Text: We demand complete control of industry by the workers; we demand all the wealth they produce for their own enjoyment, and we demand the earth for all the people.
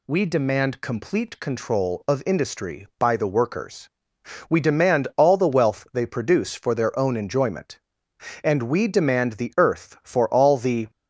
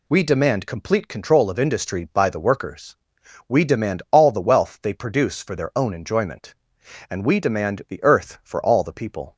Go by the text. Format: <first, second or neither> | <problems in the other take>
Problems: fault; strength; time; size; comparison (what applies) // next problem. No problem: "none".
second | stops before "people"; at 10.8 s